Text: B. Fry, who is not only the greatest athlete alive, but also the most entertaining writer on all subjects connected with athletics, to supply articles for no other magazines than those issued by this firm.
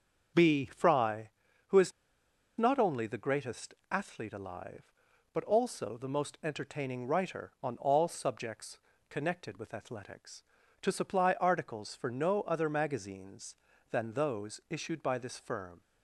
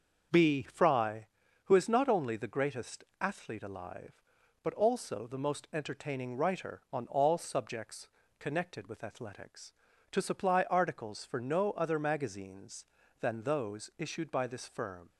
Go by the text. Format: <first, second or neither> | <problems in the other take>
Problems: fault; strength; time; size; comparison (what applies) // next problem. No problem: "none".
second | starts louder than the rest; until 1.7 s; 6 dB; also in the second // pauses between "is" and "not"; noticeable; at 1.9 s; 0.66 s long // pauses between "greatest" and "athlete"; slight; at 3.7 s; 0.18 s long; slight in the second // pauses between "subjects" and "connected"; slight; at 8.7 s; 0.30 s long; slight in the second